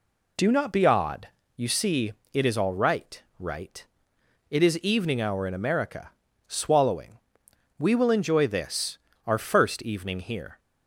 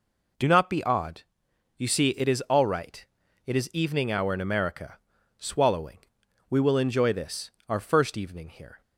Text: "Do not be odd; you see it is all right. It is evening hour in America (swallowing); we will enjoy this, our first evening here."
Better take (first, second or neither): second